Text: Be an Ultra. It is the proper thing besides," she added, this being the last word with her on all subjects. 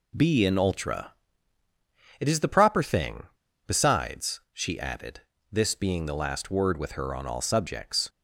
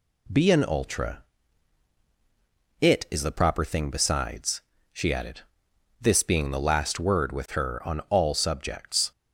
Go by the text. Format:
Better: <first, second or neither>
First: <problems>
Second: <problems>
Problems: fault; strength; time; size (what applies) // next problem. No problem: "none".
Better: second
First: pauses between "thing" and "besides"; at 3.2 s; 0.42 s long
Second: none